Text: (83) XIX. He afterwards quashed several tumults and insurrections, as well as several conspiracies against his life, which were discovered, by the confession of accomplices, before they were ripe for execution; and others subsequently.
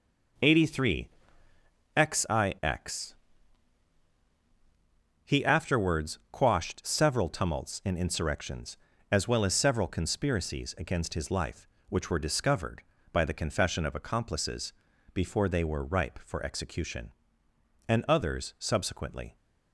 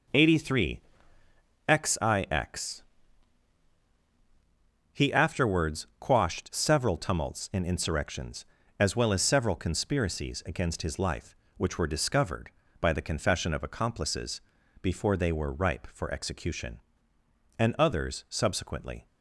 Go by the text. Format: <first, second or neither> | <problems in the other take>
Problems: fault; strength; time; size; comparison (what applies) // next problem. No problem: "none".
neither | none